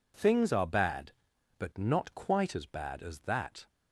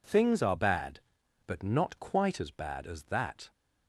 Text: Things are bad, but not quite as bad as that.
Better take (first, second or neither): neither